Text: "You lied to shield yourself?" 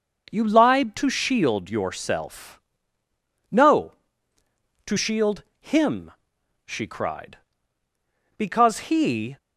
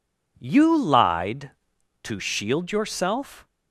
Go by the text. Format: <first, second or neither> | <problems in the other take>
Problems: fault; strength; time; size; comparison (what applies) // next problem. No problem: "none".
second | goes on to say "No to shield him she cried Because he"; strong; from 3.5 s on; 5.8 s long